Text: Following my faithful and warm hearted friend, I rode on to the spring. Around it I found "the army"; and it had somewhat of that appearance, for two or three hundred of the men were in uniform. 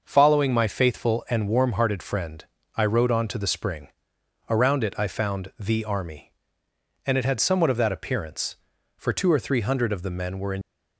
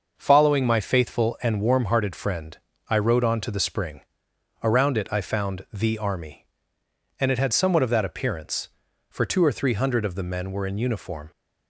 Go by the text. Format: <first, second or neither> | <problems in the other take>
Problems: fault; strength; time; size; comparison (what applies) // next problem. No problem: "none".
second | stops before "uniform"; at 10.6 s